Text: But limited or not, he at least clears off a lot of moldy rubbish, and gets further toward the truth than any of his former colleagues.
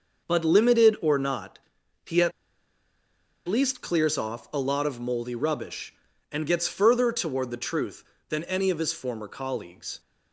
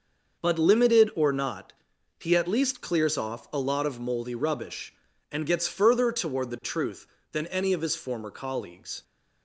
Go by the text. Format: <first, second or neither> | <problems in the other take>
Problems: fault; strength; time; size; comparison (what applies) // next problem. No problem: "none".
second | starts louder than the rest; until 1.3 s; 6 dB; also in the second // pauses between "at" and "least"; at 2.3 s; 1.1 s long